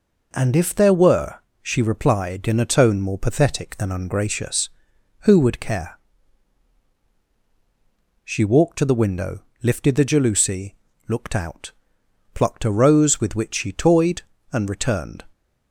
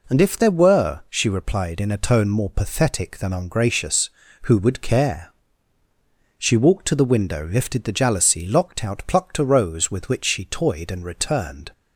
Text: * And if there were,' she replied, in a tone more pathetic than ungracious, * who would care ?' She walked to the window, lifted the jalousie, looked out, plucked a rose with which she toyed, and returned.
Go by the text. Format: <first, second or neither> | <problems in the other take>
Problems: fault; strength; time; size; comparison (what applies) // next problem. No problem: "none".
first | says "locked" for "looked"; at 8.4 s